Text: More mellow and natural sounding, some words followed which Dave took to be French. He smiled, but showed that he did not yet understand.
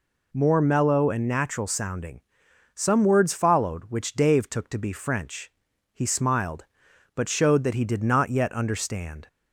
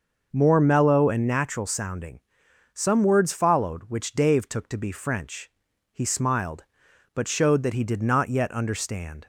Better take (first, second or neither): first